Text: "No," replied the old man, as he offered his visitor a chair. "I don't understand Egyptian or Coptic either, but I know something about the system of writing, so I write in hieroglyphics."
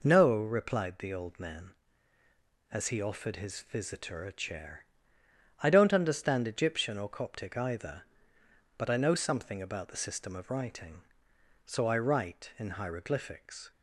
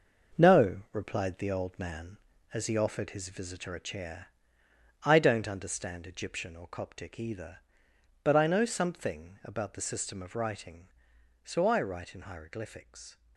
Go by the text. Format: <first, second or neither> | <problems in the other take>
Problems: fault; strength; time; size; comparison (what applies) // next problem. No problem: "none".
first | gets quieter; throughout; 7 dB